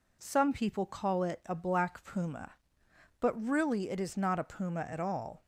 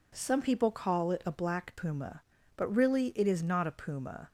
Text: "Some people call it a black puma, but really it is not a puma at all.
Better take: first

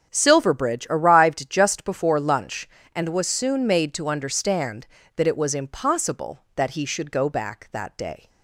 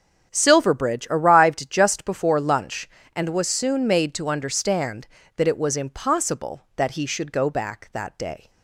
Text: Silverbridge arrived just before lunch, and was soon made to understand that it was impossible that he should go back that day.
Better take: neither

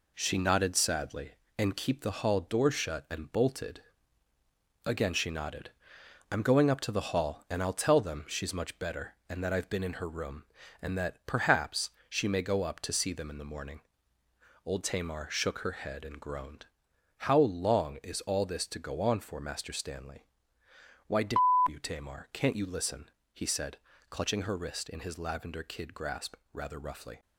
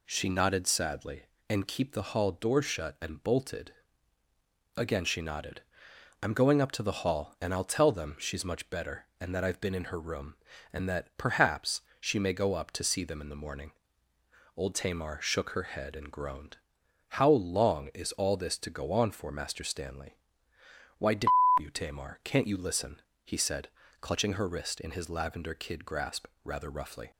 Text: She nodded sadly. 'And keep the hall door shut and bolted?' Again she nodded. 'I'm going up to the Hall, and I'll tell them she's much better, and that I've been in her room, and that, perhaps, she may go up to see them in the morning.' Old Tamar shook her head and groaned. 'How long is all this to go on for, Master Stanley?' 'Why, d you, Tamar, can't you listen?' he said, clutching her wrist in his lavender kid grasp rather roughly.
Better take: second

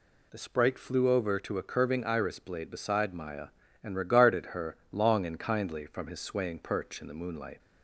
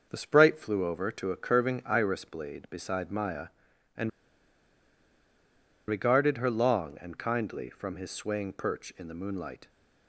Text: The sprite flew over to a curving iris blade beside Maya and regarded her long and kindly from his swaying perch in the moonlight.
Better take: first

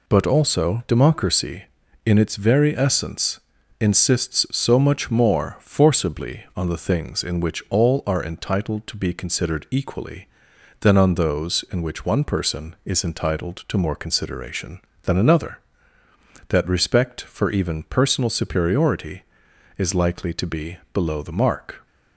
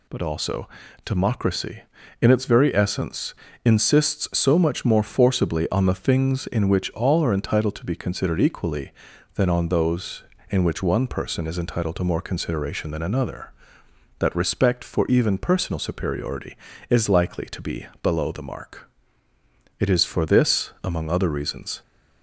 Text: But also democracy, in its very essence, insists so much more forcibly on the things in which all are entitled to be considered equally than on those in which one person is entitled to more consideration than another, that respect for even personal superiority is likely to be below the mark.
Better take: first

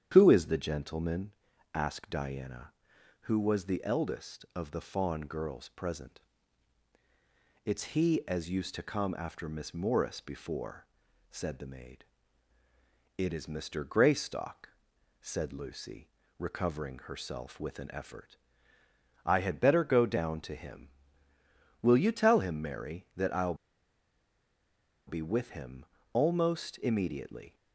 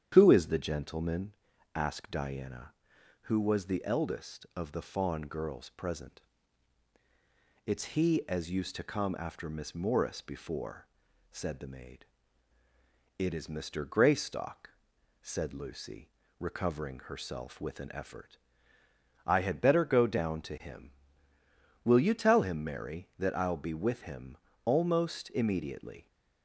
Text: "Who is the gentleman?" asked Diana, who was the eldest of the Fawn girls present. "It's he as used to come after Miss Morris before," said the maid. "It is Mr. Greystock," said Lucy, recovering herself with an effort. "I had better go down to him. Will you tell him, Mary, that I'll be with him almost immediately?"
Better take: second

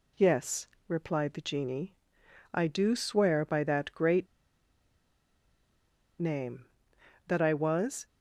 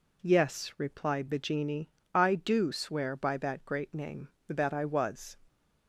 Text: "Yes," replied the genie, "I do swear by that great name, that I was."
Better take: second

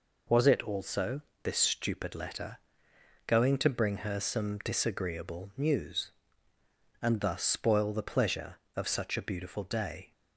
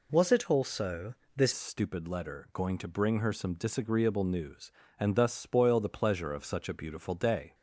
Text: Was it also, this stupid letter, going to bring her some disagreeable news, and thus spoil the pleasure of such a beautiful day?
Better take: first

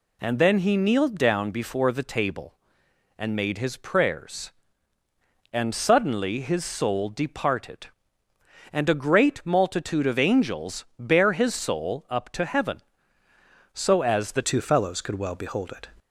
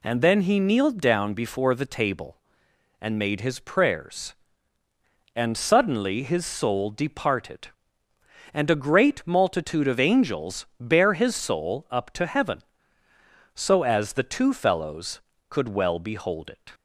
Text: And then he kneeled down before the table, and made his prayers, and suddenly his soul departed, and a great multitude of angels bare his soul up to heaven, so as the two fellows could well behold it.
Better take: second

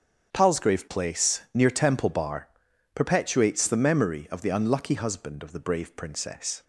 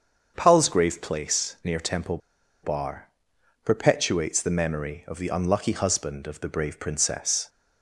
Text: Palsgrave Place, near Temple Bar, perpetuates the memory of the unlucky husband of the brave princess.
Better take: first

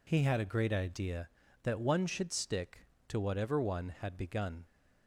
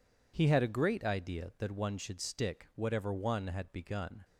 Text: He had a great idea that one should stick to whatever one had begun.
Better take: first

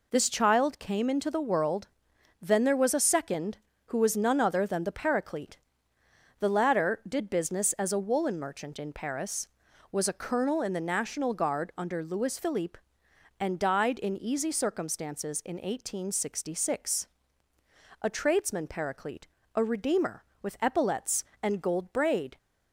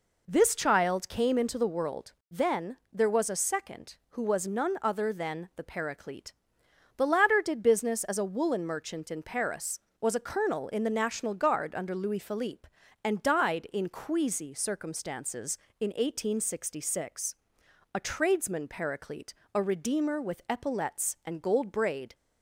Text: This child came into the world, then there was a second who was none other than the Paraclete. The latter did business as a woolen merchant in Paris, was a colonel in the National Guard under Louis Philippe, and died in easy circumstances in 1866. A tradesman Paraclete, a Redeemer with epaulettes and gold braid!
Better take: first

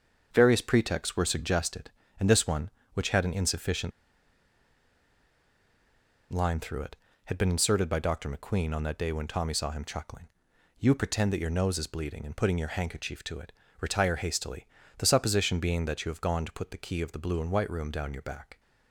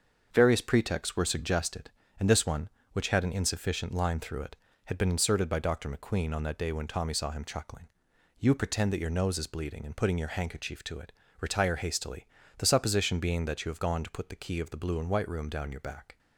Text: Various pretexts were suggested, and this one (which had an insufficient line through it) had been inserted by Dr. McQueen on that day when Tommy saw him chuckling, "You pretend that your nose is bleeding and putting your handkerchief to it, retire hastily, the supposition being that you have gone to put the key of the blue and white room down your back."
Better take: second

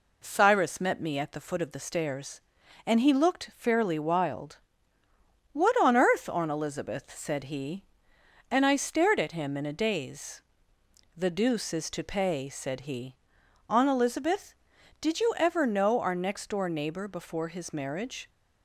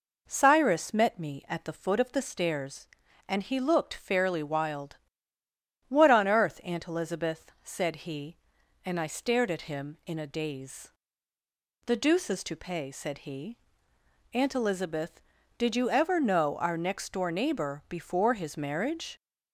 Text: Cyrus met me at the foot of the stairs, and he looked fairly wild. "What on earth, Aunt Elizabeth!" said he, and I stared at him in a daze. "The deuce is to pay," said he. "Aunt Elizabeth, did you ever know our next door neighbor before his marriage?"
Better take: neither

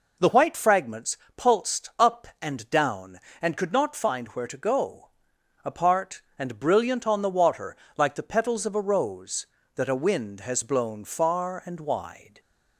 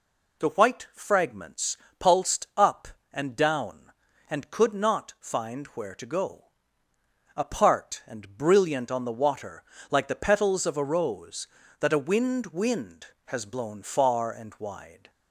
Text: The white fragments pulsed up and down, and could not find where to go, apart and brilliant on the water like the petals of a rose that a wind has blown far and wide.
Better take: first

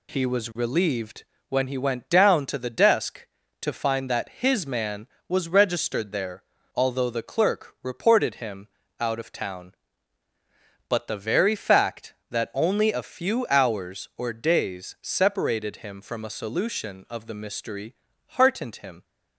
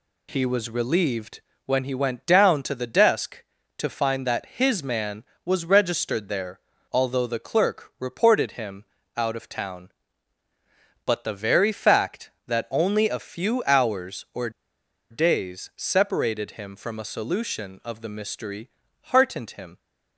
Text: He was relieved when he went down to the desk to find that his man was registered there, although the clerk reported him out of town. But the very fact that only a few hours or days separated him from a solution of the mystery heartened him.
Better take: first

